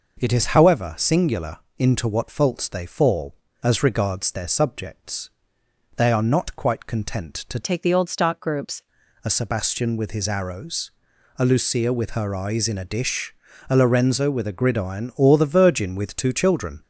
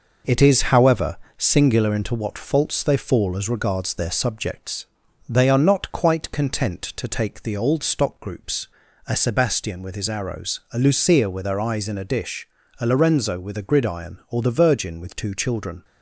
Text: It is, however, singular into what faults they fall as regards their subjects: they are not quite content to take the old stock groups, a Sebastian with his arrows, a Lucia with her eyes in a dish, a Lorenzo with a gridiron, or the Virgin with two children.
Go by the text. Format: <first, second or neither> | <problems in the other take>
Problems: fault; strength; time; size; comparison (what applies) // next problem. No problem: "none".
second | pauses between "singular" and "into"; slight; at 1.5 s; 0.20 s long // changes voice from "take" to "groups"; from 7.6 to 8.8 s; 1.2 s long